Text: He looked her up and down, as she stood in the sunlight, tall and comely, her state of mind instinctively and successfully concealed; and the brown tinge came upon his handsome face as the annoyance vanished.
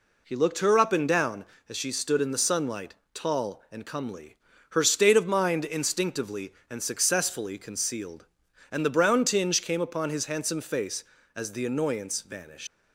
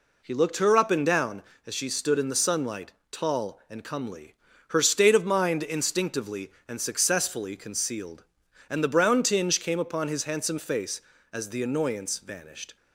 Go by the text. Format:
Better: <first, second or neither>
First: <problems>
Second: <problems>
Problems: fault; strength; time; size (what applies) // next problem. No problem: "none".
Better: second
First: leaves "vanished" unfinished; at 12.6 s; 110 ms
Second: none